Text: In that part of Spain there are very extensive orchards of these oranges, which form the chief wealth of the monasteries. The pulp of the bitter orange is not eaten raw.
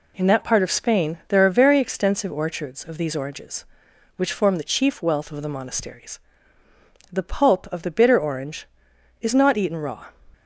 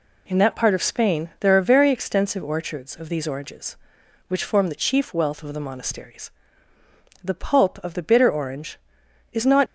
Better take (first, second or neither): first